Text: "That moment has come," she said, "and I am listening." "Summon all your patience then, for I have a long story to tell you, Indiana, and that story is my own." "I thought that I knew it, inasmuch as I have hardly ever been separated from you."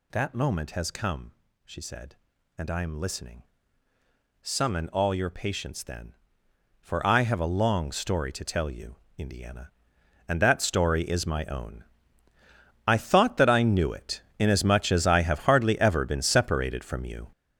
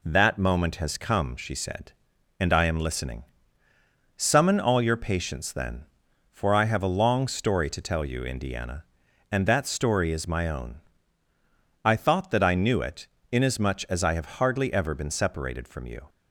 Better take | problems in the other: second | gets louder; strong; throughout; 9 dB

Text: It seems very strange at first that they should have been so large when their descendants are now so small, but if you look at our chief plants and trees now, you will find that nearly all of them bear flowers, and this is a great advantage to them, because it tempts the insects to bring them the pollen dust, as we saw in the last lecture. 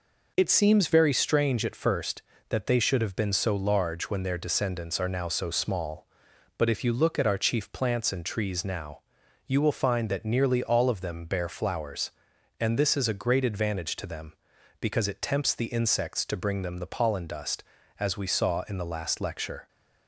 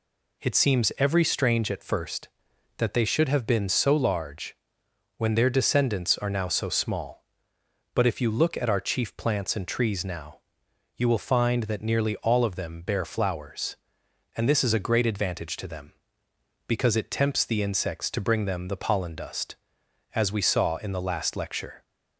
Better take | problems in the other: first | says "every" for "very"; at 0.9 s // pauses between "large" and "when"; noticeable; at 4.5 s; 0.62 s long

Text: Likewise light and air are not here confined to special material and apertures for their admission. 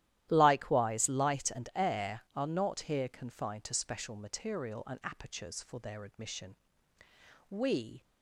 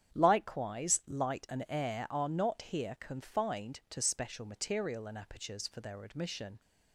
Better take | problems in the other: second | starts louder than the rest; strong; until 1.3 s; 13.5 dB; strong in the second // goes on to say "We"; from 7.4 s on; 0.54 s long

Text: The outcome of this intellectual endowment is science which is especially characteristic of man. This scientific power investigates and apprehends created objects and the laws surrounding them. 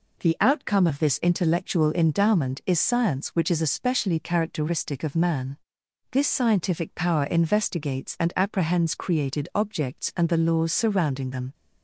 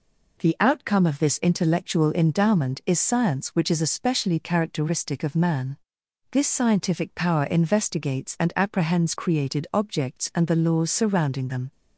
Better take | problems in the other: neither | none

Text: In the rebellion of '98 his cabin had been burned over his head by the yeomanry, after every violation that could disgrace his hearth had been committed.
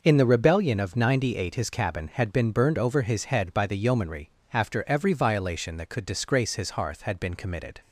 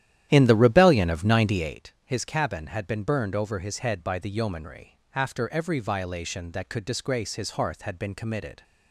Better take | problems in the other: first | starts louder than the rest; strong; until 1.8 s; 11.5 dB

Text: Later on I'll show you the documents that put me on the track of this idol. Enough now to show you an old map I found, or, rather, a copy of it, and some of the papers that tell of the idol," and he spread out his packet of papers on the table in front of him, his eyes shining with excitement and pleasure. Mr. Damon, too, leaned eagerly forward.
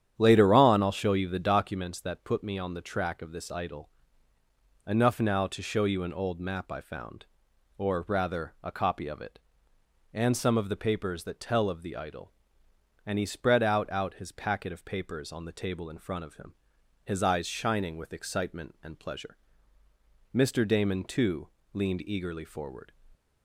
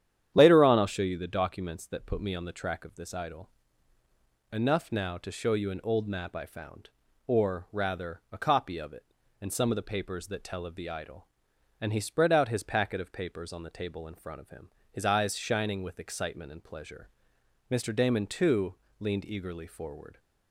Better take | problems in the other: second | starts louder than the rest; strong; until 1.1 s; 9.5 dB; strong in the second // says "out" twice; at 13.9 s

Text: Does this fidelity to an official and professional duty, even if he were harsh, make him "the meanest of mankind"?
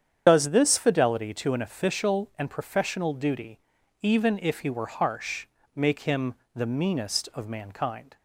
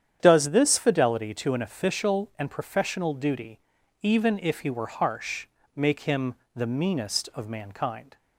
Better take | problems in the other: second | loses the start of "Does"; at 0.2 s; 60 ms // starts louder than the rest; strong; until 1.2 s; 8.5 dB; strong in the second // pauses between "him" and "the"; slight; at 6.3 s; 0.20 s long; slight in the second

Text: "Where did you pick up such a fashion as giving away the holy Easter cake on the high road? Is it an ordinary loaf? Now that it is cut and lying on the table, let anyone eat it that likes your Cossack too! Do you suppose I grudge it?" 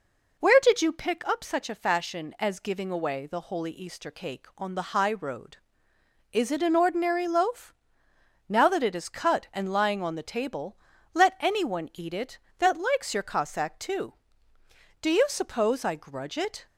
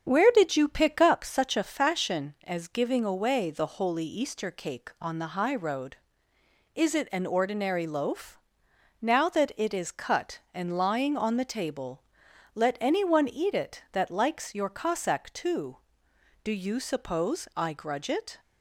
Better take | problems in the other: first | starts louder than the rest; strong; until 1.2 s; 7.5 dB

